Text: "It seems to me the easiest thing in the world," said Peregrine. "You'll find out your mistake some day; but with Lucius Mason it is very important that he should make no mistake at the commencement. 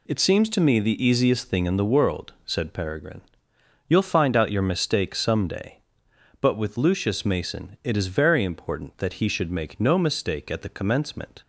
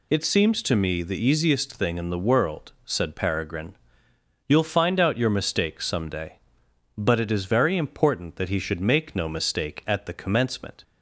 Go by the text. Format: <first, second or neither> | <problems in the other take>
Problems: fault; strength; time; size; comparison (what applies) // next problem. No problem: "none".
first | skips "with Lucius Mason"; at 7.1 s